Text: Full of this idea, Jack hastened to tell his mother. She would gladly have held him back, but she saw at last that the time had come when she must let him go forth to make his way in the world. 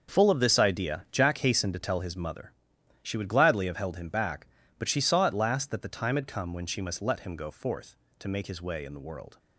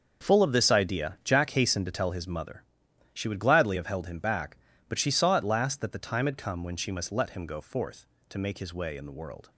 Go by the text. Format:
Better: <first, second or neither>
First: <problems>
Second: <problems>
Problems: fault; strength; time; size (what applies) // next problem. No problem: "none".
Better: neither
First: starts louder than the rest; until 1.1 s; 6.5 dB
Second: starts louder than the rest; until 1.2 s; 6.5 dB